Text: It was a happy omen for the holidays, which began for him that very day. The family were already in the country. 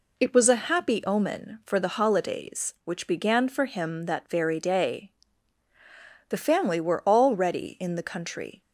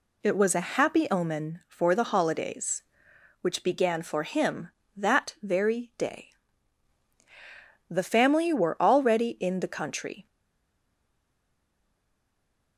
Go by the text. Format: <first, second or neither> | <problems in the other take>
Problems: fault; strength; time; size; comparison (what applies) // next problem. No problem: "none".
first | stays silent after the last word; strong; from 10.2 s on; 2.5 s long